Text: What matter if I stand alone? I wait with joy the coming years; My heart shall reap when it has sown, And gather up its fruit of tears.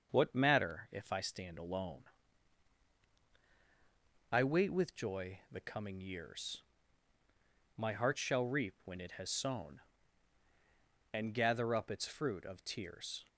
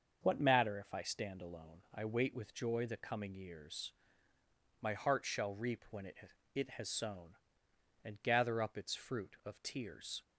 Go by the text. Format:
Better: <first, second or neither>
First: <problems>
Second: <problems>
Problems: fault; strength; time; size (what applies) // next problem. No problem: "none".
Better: first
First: starts louder than the rest; until 1.1 s; 6.5 dB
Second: starts louder than the rest; until 1.2 s; 6 dB // says "it" twice; at 6.5 s